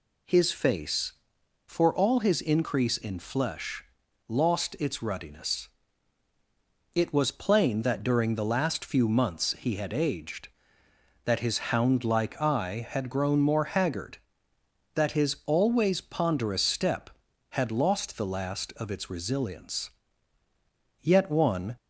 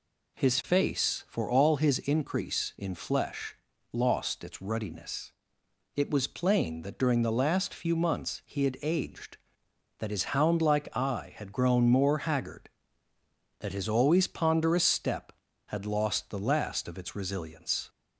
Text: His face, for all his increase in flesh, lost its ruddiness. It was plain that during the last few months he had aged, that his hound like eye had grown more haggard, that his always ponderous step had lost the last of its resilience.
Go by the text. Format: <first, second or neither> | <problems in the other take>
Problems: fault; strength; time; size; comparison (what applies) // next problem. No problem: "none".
second | goes on to say "Yet one"; noticeable; from 21.0 s on; 0.74 s long